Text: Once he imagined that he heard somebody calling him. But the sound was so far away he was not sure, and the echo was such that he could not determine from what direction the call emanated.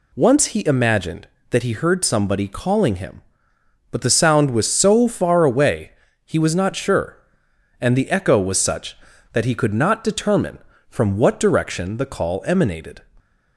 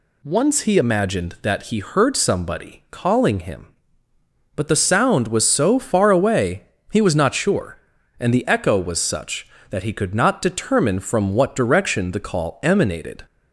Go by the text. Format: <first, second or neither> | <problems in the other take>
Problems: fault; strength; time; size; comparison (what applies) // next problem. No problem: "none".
neither | pauses between "away" and "he"; slight; the same in both